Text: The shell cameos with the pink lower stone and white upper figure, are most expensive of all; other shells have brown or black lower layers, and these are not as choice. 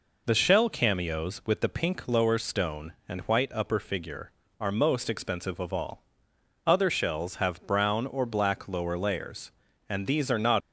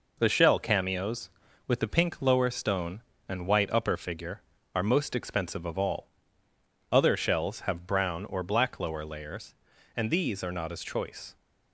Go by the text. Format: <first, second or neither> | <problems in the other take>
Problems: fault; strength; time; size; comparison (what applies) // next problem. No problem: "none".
second | stops before "as choice"; at 10.6 s